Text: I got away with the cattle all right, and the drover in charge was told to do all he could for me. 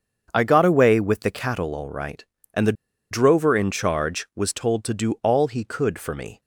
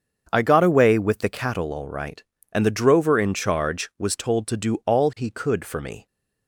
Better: second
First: starts louder than the rest; until 1.3 s; 7 dB // pauses between "the" and "drover"; at 2.7 s; 0.38 s long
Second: starts louder than the rest; until 1.3 s; 7 dB

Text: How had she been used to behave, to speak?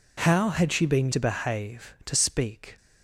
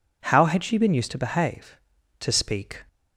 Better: second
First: skips "used"; at 1.1 s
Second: none

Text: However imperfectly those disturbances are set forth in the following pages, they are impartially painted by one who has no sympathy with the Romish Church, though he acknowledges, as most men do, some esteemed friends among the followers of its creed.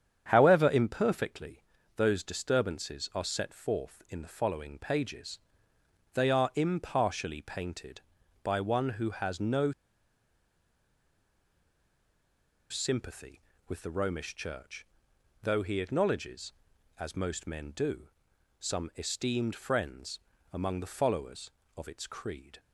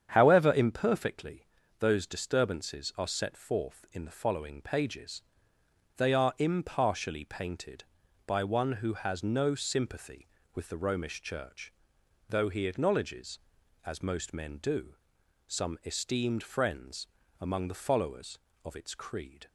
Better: second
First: starts louder than the rest; strong; until 1.2 s; 8 dB // pauses between "imperfectly" and "those"; slight; at 1.6 s; 0.32 s long // pauses between "no" and "sympathy"; strong; at 9.7 s; 2.9 s long // pauses between "friends" and "among"; slight; at 20.1 s; 0.32 s long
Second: starts louder than the rest; strong; until 1.1 s; 8.5 dB // pauses between "imperfectly" and "those"; slight; at 1.4 s; 0.32 s long // pauses between "friends" and "among"; slight; at 17.0 s; 0.32 s long

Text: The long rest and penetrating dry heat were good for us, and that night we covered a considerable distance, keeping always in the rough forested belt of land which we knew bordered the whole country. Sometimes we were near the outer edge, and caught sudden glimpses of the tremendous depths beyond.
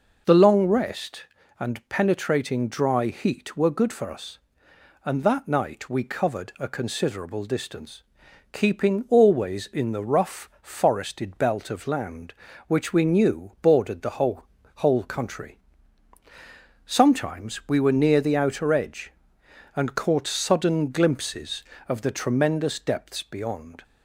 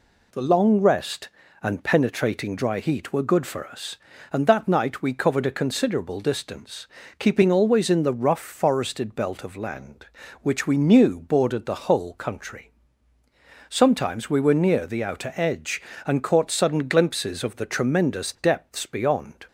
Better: second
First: says "whole" twice; at 14.7 s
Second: none

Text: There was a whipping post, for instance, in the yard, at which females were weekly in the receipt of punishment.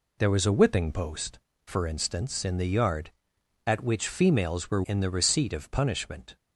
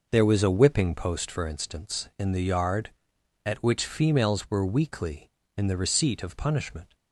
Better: second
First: skips "weekly"; at 4.8 s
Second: none

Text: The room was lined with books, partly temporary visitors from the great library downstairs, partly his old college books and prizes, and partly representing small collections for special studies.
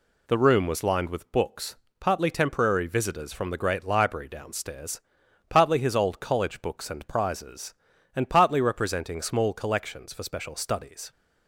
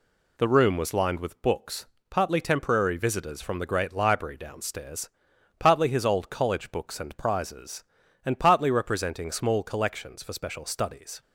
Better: neither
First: none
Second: none

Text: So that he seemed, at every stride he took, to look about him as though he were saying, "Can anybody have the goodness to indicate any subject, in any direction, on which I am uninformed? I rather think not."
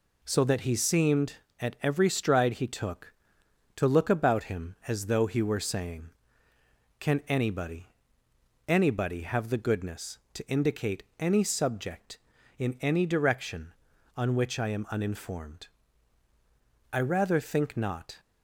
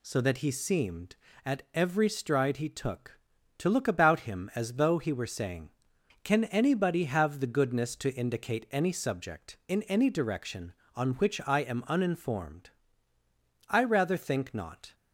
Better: second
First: says "anybody" twice; at 8.6 s // pauses between "indicate" and "any"; slight; at 11.0 s; 0.16 s long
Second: none

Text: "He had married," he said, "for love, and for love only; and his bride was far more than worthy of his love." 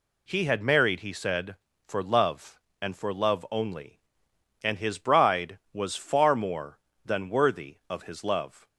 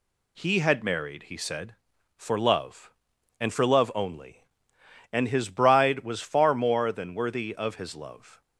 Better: neither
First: none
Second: none

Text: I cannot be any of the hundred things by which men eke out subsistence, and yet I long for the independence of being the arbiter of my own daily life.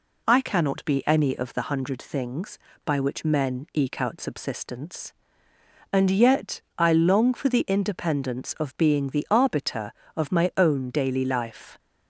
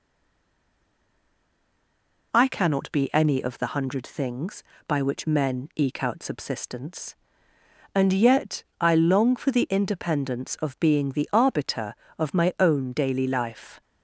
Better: first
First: pauses between "yet" and "I"; slight; at 6.6 s; 0.16 s long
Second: stays silent before the first word; until 2.3 s; 2.3 s long // pauses between "yet" and "I"; slight; at 8.6 s; 0.16 s long

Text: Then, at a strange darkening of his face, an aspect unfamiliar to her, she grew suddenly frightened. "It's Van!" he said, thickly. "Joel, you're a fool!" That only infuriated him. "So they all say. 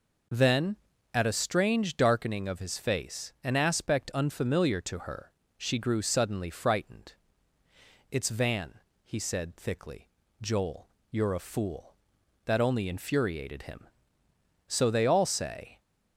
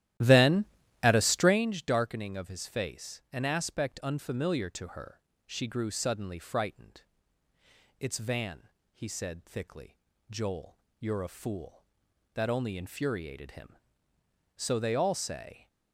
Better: first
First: none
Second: starts louder than the rest; strong; until 1.6 s; 13.5 dB

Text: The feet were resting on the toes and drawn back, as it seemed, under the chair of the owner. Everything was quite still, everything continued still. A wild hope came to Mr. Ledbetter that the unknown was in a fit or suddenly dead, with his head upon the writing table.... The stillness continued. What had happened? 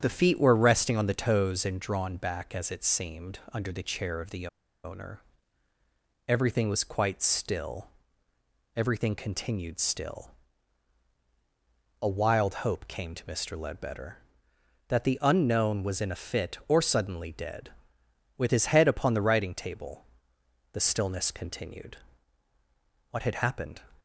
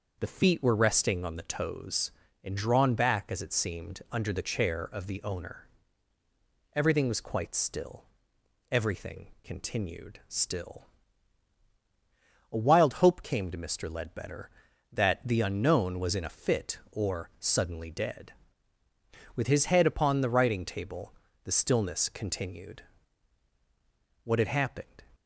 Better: second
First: starts louder than the rest; strong; until 1.0 s; 8.5 dB // pauses between "the" and "owner"; at 4.4 s; 0.36 s long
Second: none

